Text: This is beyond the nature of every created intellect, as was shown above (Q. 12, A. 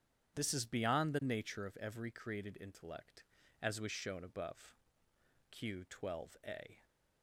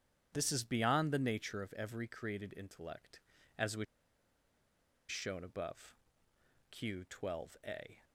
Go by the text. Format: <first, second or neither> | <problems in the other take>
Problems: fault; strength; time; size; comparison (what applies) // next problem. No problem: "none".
first | starts louder than the rest; strong; until 1.3 s; 9 dB; strong in the first // pauses between "was" and "shown"; strong; at 3.8 s; 1.2 s long